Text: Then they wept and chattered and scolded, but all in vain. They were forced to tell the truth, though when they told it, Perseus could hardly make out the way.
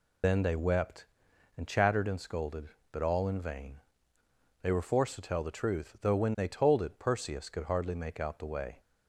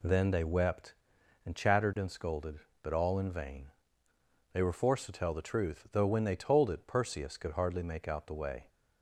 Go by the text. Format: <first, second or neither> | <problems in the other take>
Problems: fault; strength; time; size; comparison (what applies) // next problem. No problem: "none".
second | loses the start of "Then"; at 0.2 s; 115 ms